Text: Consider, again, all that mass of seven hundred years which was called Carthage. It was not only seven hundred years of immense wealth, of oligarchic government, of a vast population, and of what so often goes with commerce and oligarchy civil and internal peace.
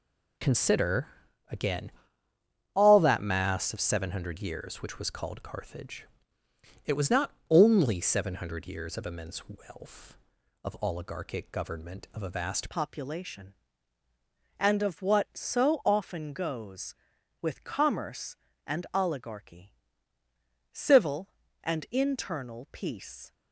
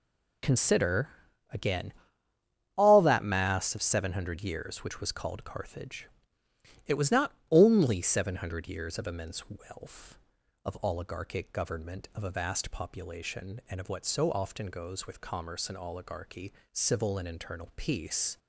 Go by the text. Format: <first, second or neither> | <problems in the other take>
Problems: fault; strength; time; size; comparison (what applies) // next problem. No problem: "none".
second | pauses between "not" and "only"; slight; at 7.3 s; 0.18 s long; slight in the second // changes voice at "population"; from 12.6 s on; 10.7 s long // pauses between "oligarchy" and "civil"; noticeable; at 19.7 s; 0.98 s long; slight in the second